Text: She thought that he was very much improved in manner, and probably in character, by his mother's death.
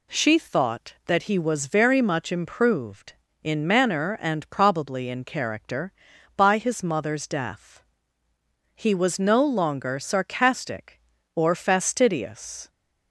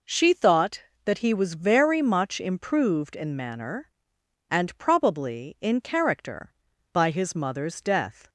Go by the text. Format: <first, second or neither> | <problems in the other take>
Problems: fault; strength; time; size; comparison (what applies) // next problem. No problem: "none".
second | goes on to say "He was no longer sarcastic or fastidious"; strong; from 8.7 s on; 3.9 s long